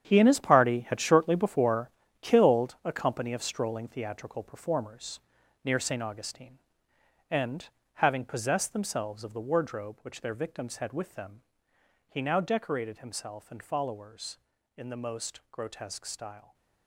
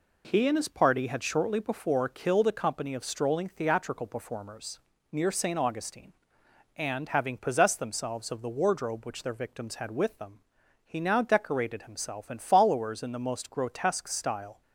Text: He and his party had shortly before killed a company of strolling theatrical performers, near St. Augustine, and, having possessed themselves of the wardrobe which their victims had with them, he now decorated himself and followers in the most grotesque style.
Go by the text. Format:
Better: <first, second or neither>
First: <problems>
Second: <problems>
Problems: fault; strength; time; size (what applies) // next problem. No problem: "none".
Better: second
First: gets quieter; strong; throughout; 11.5 dB // pauses between "before" and "killed"; slight; at 1.8 s; 0.30 s long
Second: none